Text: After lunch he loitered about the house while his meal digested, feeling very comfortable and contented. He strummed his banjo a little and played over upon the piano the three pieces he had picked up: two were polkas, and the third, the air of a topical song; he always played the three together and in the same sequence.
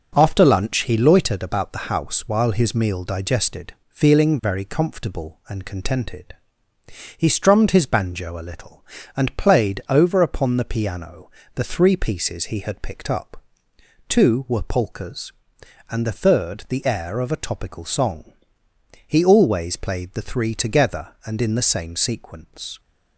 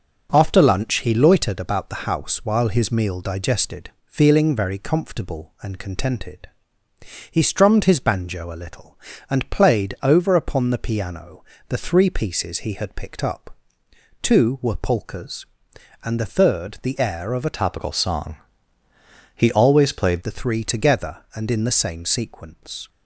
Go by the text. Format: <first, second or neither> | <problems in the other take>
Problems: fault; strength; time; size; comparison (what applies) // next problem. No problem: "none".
first | pauses between "piano" and "the"; slight; at 11.4 s; 0.24 s long; slight in the first // changes voice from "topical" to "played"; from 17.5 to 20.1 s; 2.6 s long